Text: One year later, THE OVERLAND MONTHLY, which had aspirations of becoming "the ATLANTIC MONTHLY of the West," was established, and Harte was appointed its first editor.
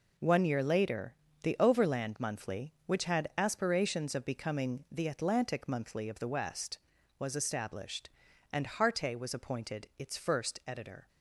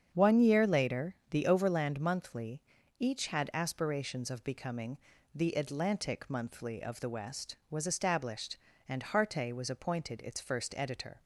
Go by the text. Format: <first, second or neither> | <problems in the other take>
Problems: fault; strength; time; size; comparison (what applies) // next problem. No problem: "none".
first | starts louder than the rest; strong; until 1.1 s; 7.5 dB // says "each" for "which"; at 2.9 s // pauses between "becoming" and "the"; slight; at 4.9 s; 0.34 s long